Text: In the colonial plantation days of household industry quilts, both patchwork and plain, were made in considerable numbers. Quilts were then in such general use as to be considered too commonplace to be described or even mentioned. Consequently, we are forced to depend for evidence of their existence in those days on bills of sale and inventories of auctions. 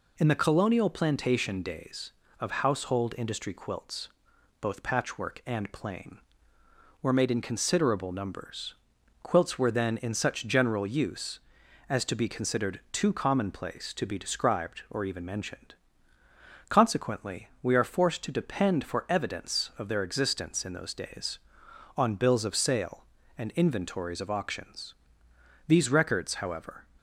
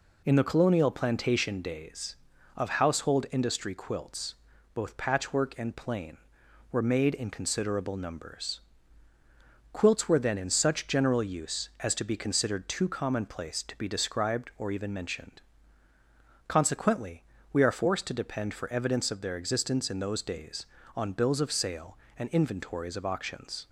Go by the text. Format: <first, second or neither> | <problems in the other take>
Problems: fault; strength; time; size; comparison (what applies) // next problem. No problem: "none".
second | goes on to say "These records however"; noticeable; from 25.6 s on; 1.1 s long